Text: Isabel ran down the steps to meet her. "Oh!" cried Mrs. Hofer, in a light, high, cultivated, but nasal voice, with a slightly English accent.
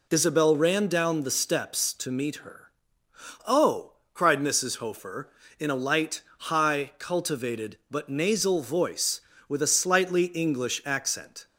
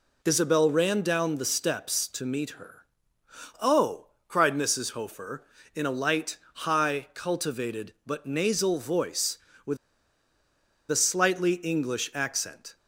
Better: first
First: none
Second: pauses between "with" and "a"; at 9.7 s; 1.1 s long

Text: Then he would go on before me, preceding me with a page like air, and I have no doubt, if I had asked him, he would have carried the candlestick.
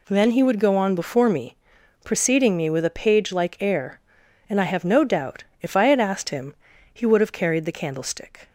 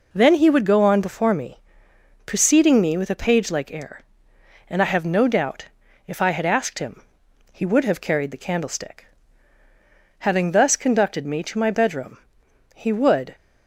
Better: first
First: none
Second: goes on to say "Having thus conducted me to my bedroom he would"; strong; from 10.1 s on; 3.1 s long

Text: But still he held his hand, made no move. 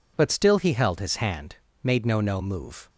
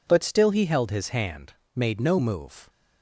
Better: second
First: says "no" twice; at 2.1 s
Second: none

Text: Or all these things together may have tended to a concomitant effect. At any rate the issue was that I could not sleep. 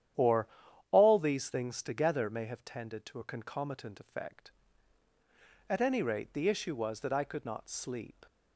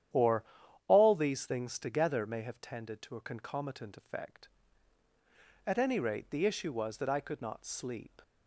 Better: neither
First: starts louder than the rest; strong; until 1.6 s; 10.5 dB // pauses between "Or" and "all"; at 0.4 s; 0.44 s long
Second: starts louder than the rest; strong; until 1.5 s; 10.5 dB // pauses between "Or" and "all"; at 0.4 s; 0.44 s long

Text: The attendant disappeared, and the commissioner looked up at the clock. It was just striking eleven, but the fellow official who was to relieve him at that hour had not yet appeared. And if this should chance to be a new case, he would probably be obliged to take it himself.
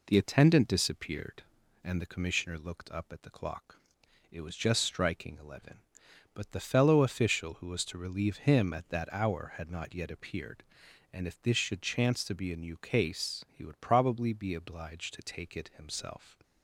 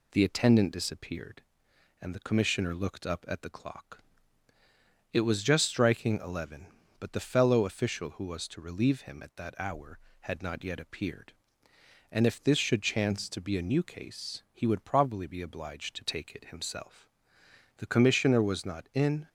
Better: first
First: none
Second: goes on to say "The commissioner was not in"; from 17.7 s on; 1.5 s long

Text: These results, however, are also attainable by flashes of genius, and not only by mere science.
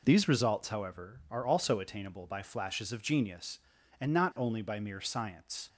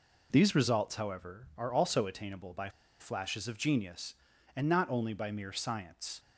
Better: first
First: none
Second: pauses between "by" and "flashes"; slight; at 2.6 s; 0.30 s long

